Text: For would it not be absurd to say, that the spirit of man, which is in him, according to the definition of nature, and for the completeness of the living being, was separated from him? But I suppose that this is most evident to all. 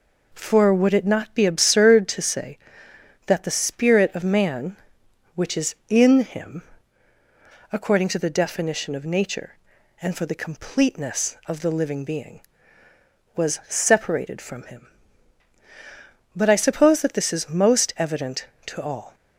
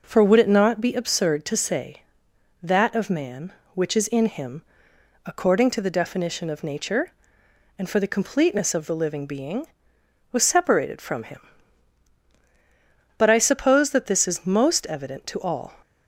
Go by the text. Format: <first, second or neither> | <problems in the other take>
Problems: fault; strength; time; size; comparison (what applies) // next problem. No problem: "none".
first | skips "the spirit"; at 2.9 s